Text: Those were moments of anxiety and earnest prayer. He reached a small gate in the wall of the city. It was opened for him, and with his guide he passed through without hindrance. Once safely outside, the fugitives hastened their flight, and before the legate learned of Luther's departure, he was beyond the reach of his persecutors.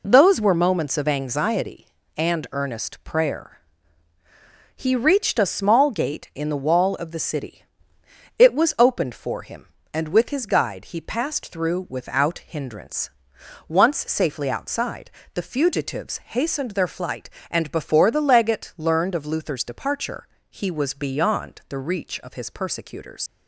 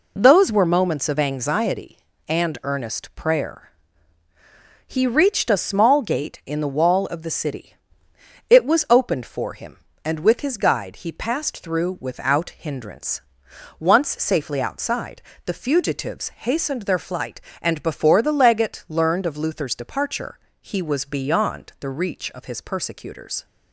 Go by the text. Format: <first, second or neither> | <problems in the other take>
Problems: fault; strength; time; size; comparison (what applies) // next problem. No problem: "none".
second | leaves "persecutors" unfinished; at 23.2 s; 75 ms